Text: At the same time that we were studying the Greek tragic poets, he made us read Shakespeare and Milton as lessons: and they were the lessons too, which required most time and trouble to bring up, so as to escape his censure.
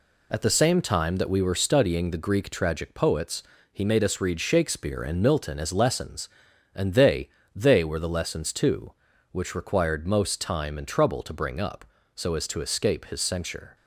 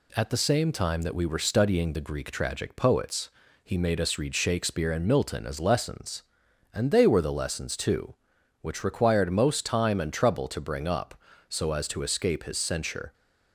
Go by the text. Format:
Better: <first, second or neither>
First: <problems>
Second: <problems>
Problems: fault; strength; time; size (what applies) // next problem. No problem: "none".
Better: second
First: says "they" twice; at 7.5 s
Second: none